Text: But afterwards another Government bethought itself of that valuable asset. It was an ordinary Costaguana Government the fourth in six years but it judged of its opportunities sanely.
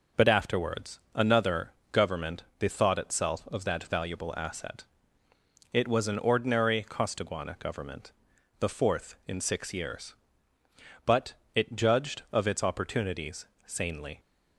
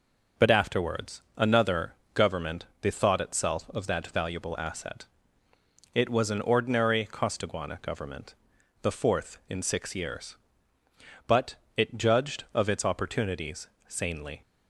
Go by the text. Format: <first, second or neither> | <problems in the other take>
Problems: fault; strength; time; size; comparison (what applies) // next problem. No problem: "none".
neither | pauses between "another" and "Government"; slight; the same in both // pauses between "Government" and "the"; noticeable; the same in both // pauses between "but" and "it"; slight; the same in both // pauses between "opportunities" and "sanely"; slight; the same in both